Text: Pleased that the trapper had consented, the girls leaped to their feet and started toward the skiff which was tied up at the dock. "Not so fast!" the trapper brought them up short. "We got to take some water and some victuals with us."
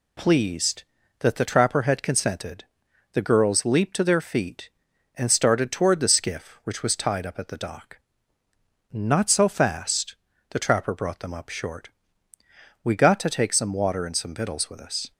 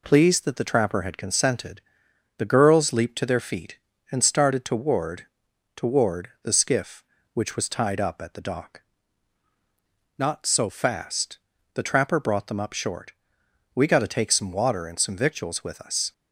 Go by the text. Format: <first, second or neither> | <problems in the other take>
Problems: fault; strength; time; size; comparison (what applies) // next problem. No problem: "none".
first | says "toward" twice; at 5.7 s